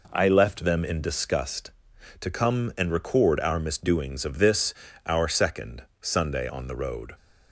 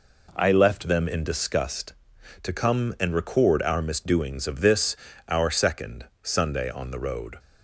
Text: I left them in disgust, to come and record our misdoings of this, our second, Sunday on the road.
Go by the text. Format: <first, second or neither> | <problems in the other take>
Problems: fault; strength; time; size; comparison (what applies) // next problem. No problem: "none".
neither | none